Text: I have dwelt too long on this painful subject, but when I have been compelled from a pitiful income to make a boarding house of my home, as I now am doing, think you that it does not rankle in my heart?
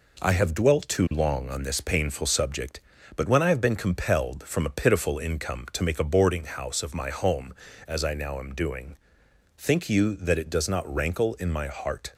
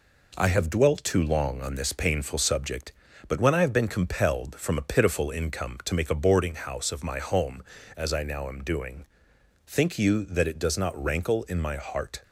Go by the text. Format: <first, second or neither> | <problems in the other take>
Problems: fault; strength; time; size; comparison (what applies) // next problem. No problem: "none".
neither | none